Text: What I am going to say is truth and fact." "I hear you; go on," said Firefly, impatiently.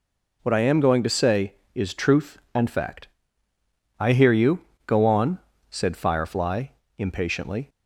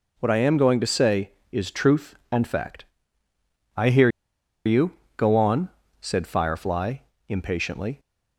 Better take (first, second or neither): first